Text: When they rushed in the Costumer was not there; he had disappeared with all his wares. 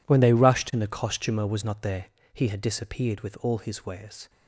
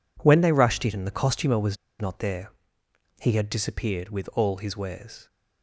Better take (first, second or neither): first